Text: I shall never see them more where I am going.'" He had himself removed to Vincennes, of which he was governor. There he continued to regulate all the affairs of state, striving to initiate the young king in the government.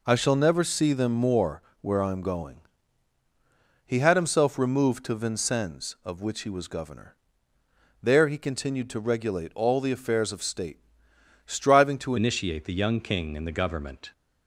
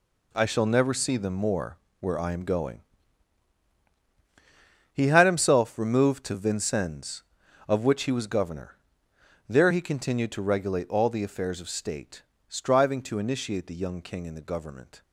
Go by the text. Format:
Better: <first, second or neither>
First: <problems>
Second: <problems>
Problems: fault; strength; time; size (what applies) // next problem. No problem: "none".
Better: second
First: pauses between "more" and "where"; slight; at 1.6 s; 0.18 s long // changes voice at "initiate"; from 12.1 s on; 2.0 s long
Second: pauses between "more" and "where"; slight; at 1.7 s; 0.22 s long